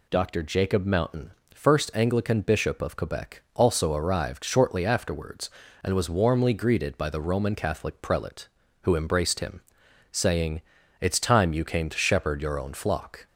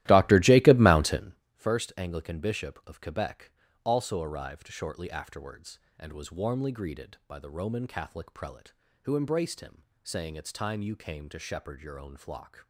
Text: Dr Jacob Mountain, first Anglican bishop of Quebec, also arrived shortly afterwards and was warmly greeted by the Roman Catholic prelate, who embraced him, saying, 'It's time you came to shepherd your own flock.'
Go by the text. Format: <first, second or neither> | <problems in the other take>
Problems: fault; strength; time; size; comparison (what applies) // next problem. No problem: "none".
first | starts louder than the rest; strong; until 1.4 s; 15.5 dB